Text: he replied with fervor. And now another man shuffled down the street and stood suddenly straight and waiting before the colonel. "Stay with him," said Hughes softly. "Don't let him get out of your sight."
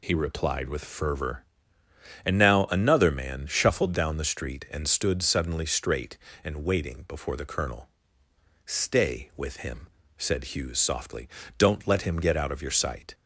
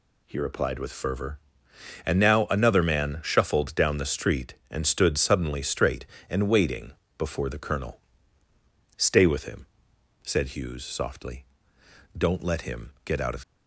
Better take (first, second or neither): first